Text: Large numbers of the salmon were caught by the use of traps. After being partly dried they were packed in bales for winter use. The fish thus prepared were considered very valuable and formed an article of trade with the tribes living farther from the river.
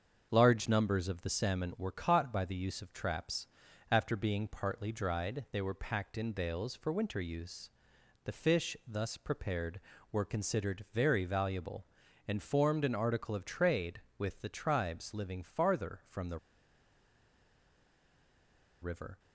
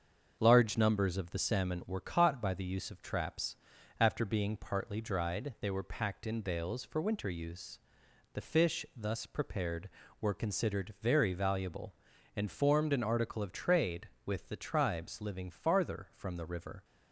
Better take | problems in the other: second | starts louder than the rest; until 1.3 s; 7 dB; also in the second // pauses between "the" and "river"; strong; at 16.3 s; 2.4 s long

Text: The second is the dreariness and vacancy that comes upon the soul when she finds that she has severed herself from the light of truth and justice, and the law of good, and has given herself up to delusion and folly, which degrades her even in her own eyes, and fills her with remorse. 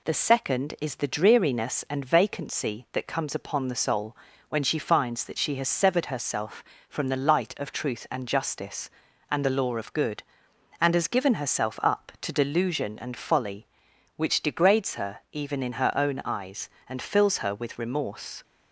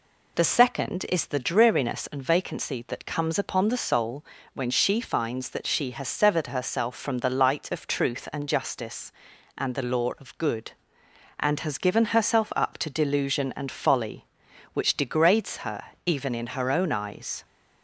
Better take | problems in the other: first | pauses between "soul" and "when"; slight; at 4.2 s; 0.28 s long; slight in the first // pauses between "her" and "even"; slight; at 15.8 s; 0.24 s long // stops before "and fills her with remorse"; at 17.4 s

